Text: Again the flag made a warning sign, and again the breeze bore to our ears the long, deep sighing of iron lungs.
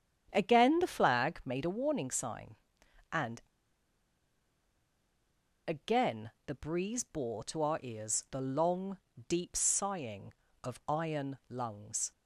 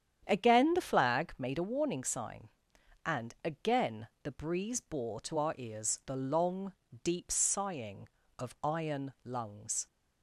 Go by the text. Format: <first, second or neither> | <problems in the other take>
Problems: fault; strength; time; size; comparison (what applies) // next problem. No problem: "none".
second | starts louder than the rest; strong; until 1.3 s; 9 dB; strong in the second // pauses between "and" and "again"; strong; at 3.4 s; 2.2 s long // pauses between "again" and "the"; slight; at 6.2 s; 0.16 s long; slight in the second